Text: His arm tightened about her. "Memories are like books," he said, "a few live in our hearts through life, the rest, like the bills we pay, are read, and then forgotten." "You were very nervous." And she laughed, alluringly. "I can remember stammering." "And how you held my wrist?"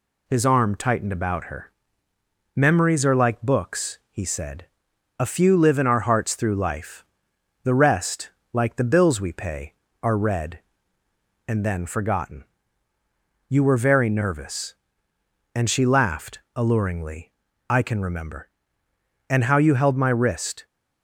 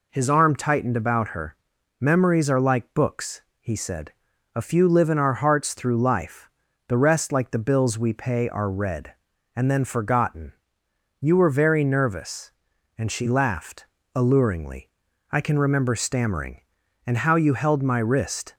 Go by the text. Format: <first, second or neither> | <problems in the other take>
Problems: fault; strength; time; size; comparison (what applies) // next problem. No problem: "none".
second | skips "stammering"; at 18.8 s